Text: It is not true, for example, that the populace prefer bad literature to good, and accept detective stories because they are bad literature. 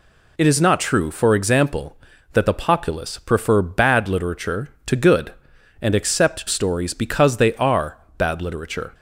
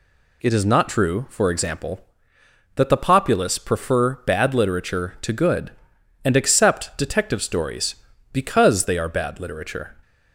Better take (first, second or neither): second